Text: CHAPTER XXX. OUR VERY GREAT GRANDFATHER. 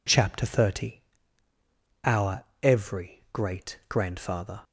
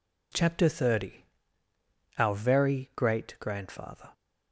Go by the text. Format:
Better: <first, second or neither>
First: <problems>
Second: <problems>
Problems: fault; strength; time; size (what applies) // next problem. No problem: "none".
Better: second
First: says "Every" for "VERY"; at 2.6 s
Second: none